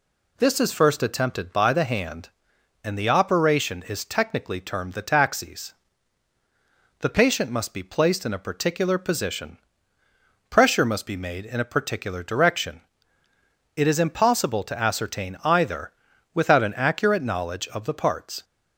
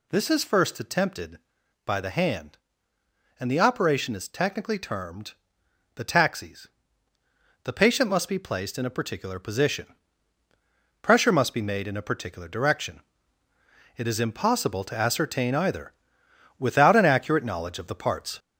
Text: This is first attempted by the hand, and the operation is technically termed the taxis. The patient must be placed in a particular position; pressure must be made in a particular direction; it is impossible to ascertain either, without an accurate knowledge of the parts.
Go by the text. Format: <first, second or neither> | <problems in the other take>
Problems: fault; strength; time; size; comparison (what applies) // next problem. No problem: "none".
first | gets louder; throughout; 3.5 dB // pauses between "termed" and "the"; noticeable; at 5.3 s; 0.64 s long